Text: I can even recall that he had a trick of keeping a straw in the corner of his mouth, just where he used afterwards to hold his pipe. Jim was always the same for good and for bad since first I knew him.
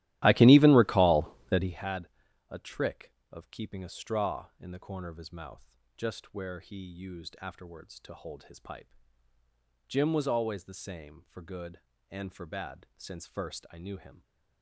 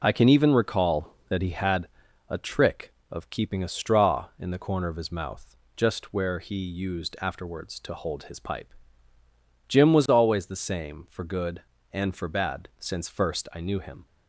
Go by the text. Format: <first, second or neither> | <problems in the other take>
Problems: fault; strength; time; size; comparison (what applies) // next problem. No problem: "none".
second | starts louder than the rest; strong; until 1.8 s; 15 dB // pauses between "had" and "a"; at 2.0 s; 0.42 s long; also in the second